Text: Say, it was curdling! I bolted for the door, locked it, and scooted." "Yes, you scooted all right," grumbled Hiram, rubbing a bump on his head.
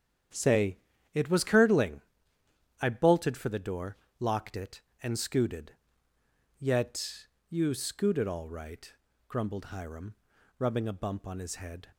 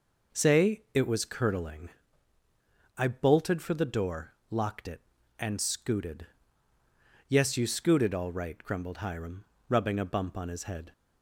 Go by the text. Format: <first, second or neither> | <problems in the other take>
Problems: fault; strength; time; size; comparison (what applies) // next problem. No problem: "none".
second | starts louder than the rest; strong; until 1.6 s; 9 dB // says "Yet" for "Yes"; at 6.5 s